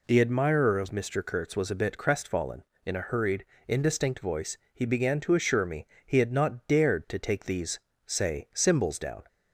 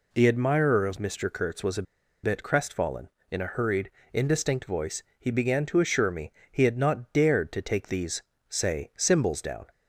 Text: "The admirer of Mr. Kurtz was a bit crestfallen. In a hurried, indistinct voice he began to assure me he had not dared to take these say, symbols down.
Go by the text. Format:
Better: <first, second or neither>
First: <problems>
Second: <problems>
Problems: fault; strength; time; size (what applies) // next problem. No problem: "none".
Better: first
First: pauses between "voice" and "he"; slight; at 4.5 s; 0.16 s long // pauses between "me" and "he"; slight; at 5.8 s; 0.20 s long // pauses between "these" and "say"; slight; at 7.8 s; 0.26 s long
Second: pauses between "a" and "bit"; at 1.8 s; 0.40 s long // pauses between "voice" and "he"; slight; at 5.0 s; 0.16 s long // pauses between "me" and "he"; slight; at 6.3 s; 0.20 s long // pauses between "these" and "say"; slight; at 8.2 s; 0.26 s long